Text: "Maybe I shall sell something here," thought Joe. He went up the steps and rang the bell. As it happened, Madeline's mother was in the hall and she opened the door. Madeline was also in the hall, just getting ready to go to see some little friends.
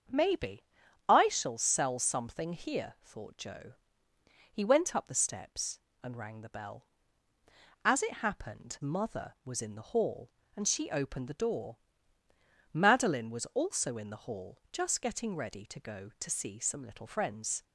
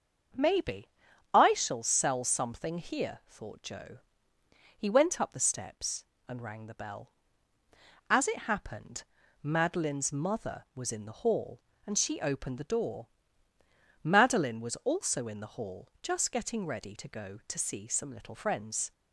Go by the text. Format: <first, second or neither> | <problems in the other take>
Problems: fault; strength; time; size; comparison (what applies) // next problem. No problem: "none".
second | starts louder than the rest; until 1.5 s; 7 dB; also in the second // pauses between "Maybe" and "I"; at 0.6 s; 0.44 s long; also in the second // skips "Madeline's"; at 8.7 s